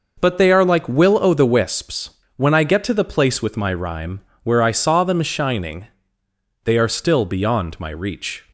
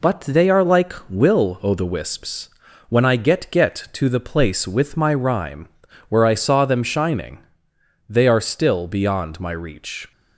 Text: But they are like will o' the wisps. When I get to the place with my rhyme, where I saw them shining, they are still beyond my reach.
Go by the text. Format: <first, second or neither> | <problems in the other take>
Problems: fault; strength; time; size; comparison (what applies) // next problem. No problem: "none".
first | says "get" twice; at 3.5 s